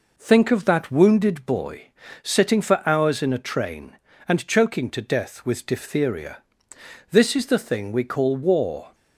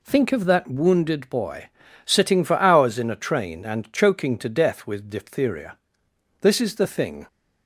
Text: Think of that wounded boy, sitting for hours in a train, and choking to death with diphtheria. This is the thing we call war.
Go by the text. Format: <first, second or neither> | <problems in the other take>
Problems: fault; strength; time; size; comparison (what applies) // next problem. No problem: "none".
first | stops before "we call war"; at 7.2 s